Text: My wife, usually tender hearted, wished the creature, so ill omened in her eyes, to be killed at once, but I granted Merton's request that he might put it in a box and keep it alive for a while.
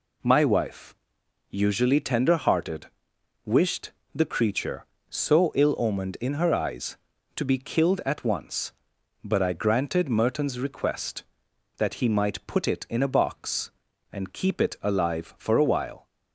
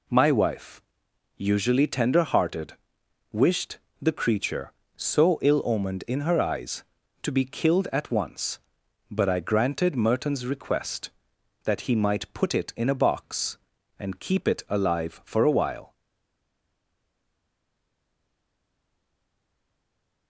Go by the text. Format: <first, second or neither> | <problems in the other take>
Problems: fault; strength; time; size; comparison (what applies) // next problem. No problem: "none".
first | pauses between "wished" and "the"; slight; at 3.7 s; 0.22 s long; slight in the first // stays silent after the last word; strong; from 15.9 s on; 4.3 s long